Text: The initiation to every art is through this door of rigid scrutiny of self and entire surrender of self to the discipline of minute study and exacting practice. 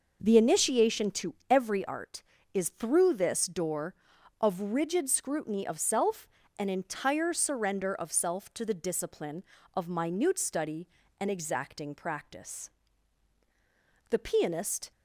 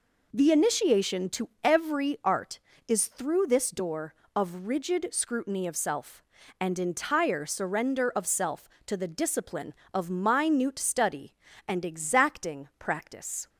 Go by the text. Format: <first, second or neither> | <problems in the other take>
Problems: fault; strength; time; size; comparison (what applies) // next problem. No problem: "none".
second | pauses between "to" and "every"; slight; at 1.3 s; 0.16 s long // goes on to say "The pianist"; noticeable; from 14.1 s on; 0.80 s long